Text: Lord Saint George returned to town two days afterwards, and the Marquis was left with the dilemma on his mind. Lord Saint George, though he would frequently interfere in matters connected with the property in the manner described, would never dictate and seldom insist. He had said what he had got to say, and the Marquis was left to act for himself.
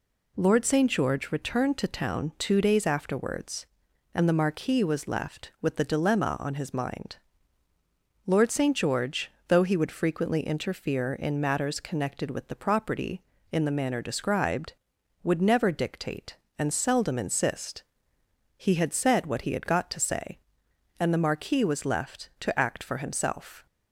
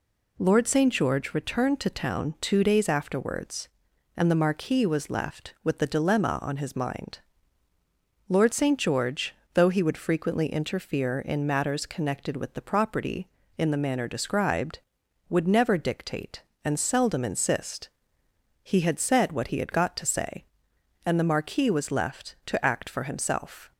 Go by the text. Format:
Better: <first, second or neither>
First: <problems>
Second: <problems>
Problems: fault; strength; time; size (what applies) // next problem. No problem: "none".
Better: neither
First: none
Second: none